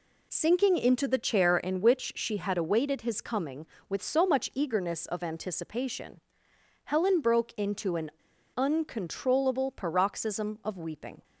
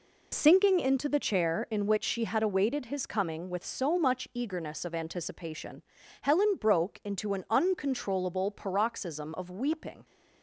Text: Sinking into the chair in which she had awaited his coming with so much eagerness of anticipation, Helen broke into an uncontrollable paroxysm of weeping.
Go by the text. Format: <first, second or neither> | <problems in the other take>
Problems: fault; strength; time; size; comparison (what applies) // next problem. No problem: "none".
second | pauses between "an" and "uncontrollable"; at 8.1 s; 0.45 s long